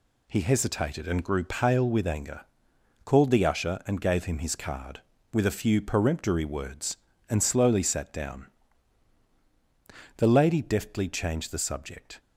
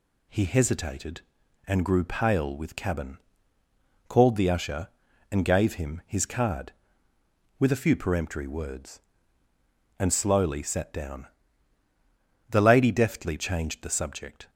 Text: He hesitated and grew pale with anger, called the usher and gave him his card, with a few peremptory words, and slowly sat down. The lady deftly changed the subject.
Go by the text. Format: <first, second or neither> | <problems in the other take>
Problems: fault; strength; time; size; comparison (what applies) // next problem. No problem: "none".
first | says "cabin" for "anger"; at 2.7 s